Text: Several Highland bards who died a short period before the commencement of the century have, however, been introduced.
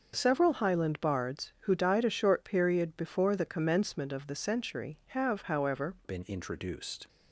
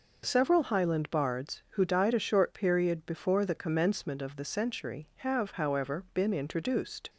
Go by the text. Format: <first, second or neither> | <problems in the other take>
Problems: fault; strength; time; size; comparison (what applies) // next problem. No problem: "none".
second | changes voice at "been"; from 6.0 s on; 1.0 s long